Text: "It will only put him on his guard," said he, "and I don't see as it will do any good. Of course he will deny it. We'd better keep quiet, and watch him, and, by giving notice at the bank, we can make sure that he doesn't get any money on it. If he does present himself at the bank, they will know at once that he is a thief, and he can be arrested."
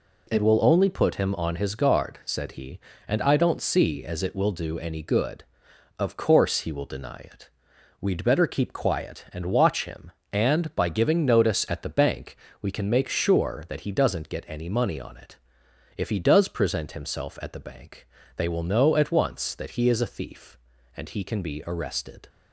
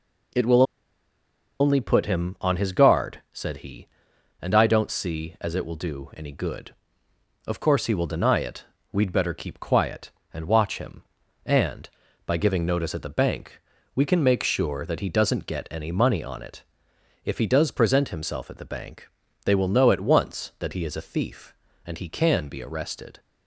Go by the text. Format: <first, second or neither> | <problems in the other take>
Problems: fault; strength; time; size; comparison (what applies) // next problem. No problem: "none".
first | pauses between "will" and "only"; noticeable; at 0.6 s; 0.97 s long